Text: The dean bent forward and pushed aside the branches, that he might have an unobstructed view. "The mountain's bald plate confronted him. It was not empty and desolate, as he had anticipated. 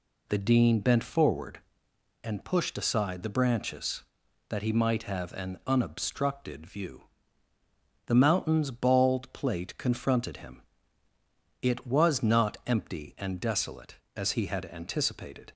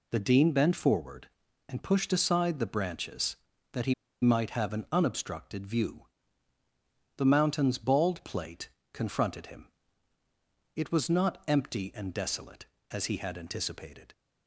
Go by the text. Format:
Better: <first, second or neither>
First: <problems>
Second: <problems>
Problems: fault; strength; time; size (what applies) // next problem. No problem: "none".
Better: first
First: none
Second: pauses between "he" and "might"; slight; at 3.9 s; 0.28 s long // pauses between "plate" and "confronted"; slight; at 8.6 s; 0.24 s long